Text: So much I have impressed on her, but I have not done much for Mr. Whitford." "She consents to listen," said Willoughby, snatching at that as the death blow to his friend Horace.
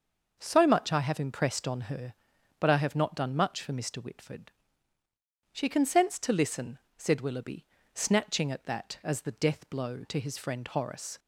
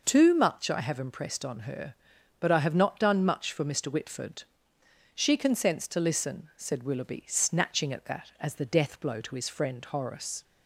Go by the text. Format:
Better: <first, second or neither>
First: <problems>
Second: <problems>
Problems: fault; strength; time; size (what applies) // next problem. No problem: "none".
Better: first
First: none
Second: says "Too" for "So"; at 0.0 s